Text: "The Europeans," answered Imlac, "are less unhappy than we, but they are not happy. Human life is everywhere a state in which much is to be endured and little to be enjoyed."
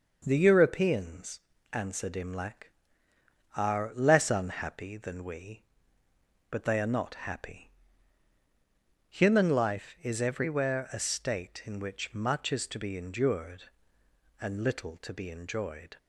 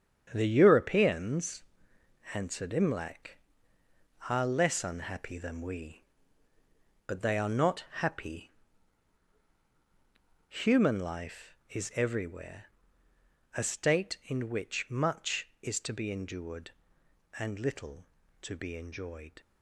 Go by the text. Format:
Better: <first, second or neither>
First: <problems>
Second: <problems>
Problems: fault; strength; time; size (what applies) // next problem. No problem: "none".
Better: first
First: none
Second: gets quieter; strong; throughout; 8.5 dB // pauses between "not" and "happy"; slight; at 7.8 s; 0.18 s long // pauses between "everywhere" and "a"; noticeable; at 12.6 s; 0.88 s long